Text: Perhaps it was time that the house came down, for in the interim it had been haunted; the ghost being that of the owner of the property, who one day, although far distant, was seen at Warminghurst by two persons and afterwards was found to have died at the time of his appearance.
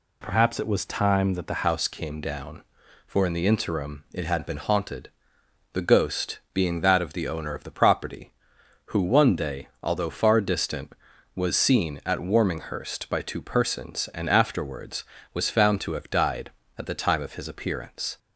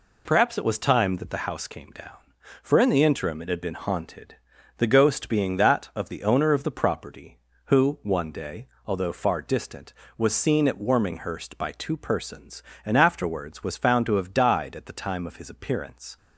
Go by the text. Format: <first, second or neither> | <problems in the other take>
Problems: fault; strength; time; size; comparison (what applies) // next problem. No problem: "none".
second | changes voice at "house"; from 1.6 s on; 16.5 s long // pauses between "ghost" and "being"; slight; at 6.3 s; 0.16 s long